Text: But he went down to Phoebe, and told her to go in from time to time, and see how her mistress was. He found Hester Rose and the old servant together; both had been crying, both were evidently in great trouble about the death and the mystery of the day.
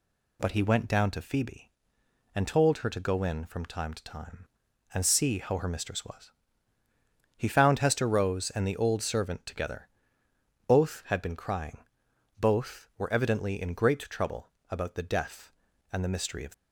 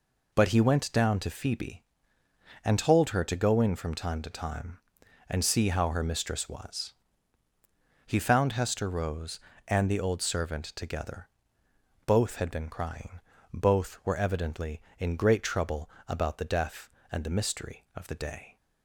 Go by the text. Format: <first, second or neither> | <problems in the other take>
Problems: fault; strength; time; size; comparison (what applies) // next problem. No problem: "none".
second | pauses between "trouble" and "about"; slight; at 14.4 s; 0.22 s long; slight in the second // stops before "the day"; at 16.5 s